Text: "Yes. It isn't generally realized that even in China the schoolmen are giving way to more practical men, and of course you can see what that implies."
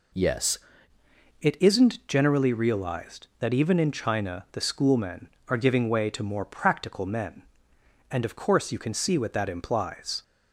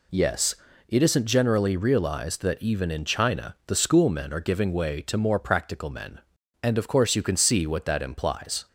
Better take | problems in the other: second | changes voice at "It"; from 1.4 s on; 8.8 s long

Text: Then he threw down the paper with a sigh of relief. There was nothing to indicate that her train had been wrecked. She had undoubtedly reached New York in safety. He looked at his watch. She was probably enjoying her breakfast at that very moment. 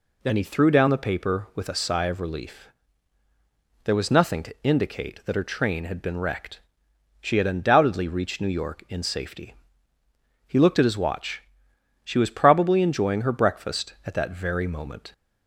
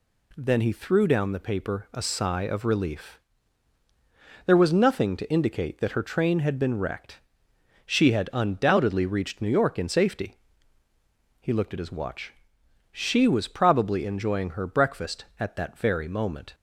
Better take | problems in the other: first | skips "with"; at 1.8 s

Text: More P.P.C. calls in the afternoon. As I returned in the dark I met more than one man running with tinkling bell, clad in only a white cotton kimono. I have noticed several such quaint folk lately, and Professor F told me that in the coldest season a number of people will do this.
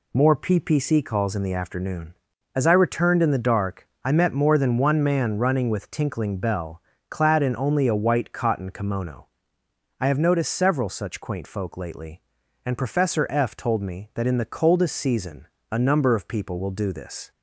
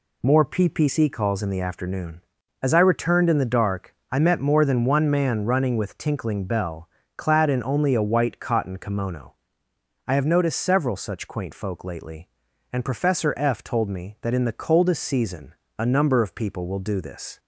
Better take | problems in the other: neither | pauses between "dark" and "I"; slight; the same in both // pauses between "season" and "a"; slight; the same in both

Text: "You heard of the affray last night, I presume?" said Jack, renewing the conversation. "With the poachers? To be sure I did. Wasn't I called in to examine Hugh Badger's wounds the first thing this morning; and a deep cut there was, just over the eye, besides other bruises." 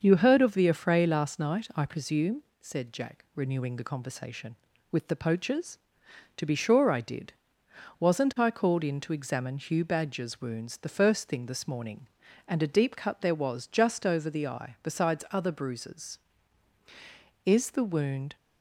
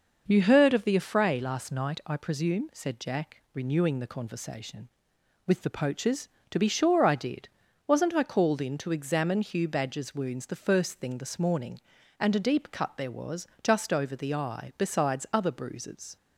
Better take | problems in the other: second | starts louder than the rest; until 1.0 s; 6.5 dB // goes on to say "Is the wound"; noticeable; from 17.4 s on; 0.90 s long

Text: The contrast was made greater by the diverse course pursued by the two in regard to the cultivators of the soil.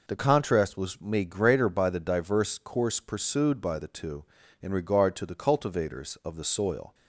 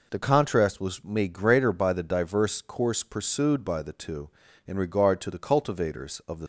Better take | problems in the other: first | stops before "soil"; at 6.4 s

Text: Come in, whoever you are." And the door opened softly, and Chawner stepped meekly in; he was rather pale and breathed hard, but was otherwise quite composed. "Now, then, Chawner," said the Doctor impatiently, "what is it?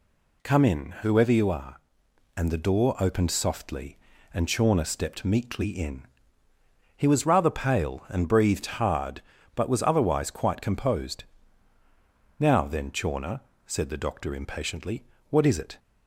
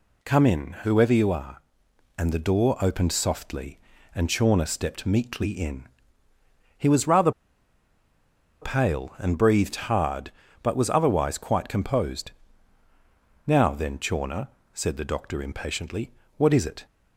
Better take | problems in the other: first | pauses between "rather" and "pale"; strong; at 7.3 s; 1.3 s long

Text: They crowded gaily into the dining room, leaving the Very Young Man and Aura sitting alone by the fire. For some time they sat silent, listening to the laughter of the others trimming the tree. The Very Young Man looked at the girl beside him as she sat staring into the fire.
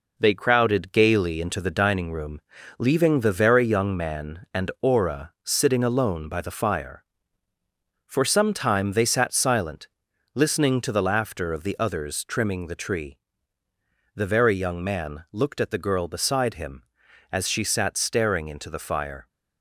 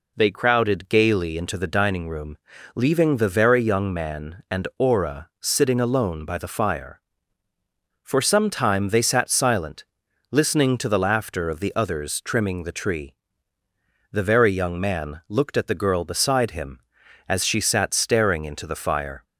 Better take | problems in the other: second | gets quieter; noticeable; throughout; 4.5 dB

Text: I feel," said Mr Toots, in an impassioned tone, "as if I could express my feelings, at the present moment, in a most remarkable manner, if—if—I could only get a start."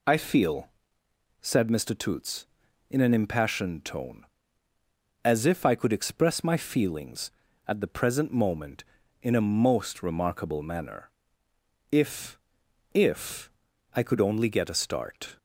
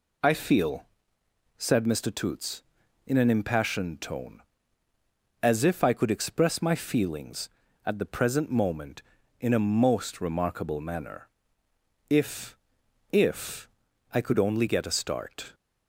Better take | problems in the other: neither | none

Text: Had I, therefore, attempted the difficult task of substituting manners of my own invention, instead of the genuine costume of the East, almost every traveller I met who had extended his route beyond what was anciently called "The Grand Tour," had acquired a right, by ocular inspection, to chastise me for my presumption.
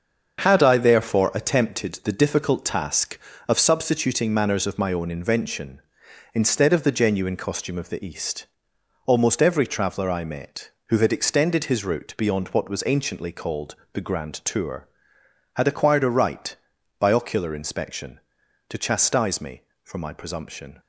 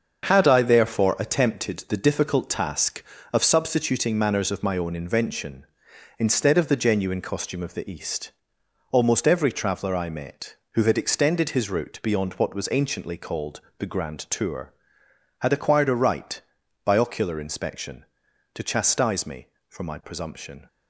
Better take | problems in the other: neither | starts louder than the rest; the same in both // pauses between "called" and "The"; slight; the same in both

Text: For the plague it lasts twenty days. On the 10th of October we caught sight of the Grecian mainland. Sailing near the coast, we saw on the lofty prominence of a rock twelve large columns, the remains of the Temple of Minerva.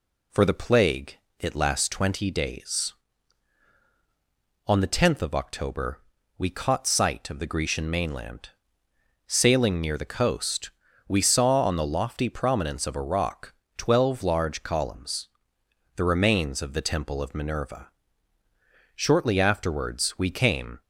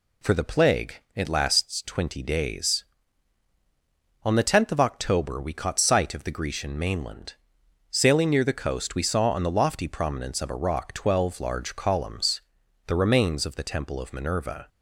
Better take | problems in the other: second | pauses between "plague" and "it"; slight; at 1.1 s; 0.22 s long; slight in the second // pauses between "October" and "we"; at 5.9 s; 0.38 s long // pauses between "rock" and "twelve"; slight; at 13.5 s; 0.24 s long // goes on to say "Shortly afterwards we came"; strong; from 18.9 s on; 1.8 s long

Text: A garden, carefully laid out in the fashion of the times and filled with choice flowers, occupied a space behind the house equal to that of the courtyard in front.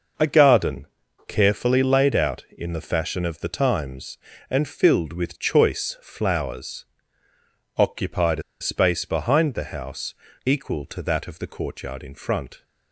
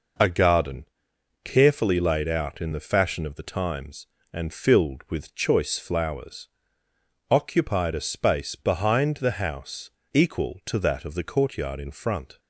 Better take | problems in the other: second | pauses between "a" and "space"; slight; at 8.4 s; 0.18 s long // pauses between "house" and "equal"; slight; at 10.1 s; 0.32 s long; slight in the second

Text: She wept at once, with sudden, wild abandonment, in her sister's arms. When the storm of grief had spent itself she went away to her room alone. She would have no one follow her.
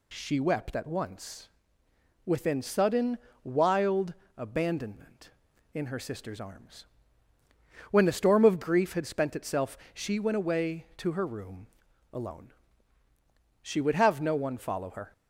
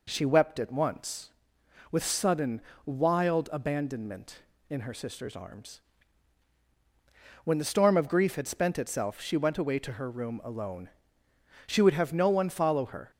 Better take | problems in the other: second | says "within" for "with"; at 2.2 s // pauses between "wild" and "abandonment"; slight; at 4.1 s; 0.24 s long // pauses between "itself" and "she"; slight; at 9.7 s; 0.16 s long // pauses between "room" and "alone"; noticeable; at 11.6 s; 0.46 s long

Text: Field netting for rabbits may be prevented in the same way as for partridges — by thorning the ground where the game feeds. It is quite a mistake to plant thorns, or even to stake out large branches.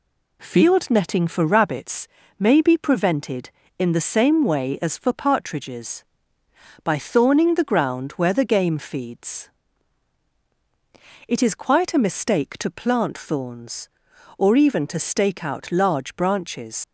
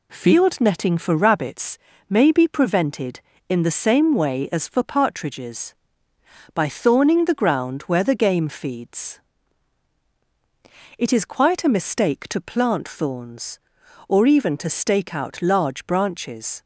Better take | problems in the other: second | pauses between "rabbits" and "may"; slight; at 2.0 s; 0.30 s long; slight in the second // leaves "branches" unfinished; at 16.8 s; 65 ms

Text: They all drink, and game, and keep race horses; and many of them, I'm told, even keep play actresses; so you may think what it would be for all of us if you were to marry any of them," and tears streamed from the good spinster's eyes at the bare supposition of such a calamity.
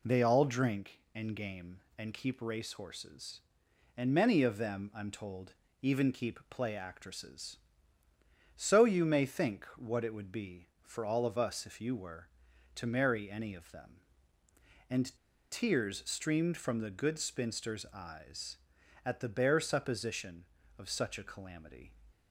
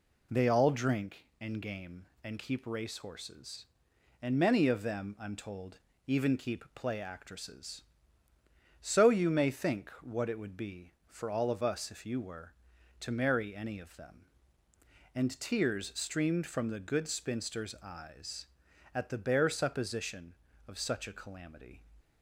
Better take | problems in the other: second | pauses between "and" and "tears"; slight; at 15.1 s; 0.35 s long

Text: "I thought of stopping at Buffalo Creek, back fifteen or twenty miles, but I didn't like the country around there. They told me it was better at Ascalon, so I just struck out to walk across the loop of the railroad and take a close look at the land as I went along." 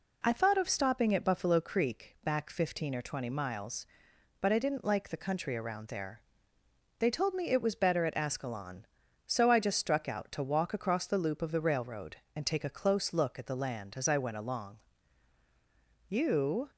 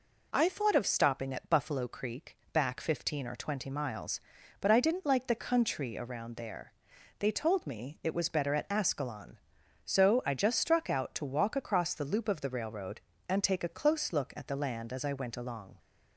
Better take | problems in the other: second | goes on to say "You"; noticeable; from 16.0 s on; 0.64 s long

